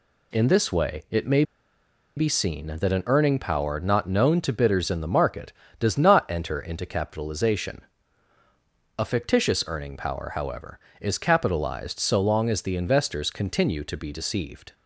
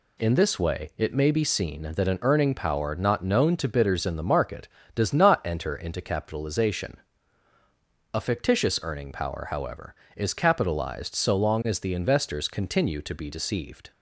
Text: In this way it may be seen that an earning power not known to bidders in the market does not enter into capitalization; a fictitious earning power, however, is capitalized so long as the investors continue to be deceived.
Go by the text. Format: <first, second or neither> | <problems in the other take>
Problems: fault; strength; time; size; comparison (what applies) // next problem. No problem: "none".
second | pauses between "may" and "be"; noticeable; at 1.4 s; 0.74 s long